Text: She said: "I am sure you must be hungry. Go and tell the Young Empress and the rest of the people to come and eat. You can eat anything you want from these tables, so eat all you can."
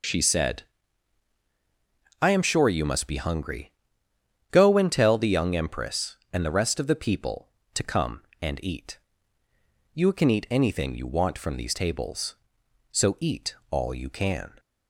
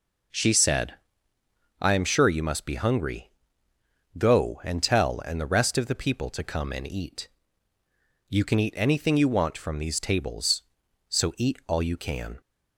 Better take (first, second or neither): first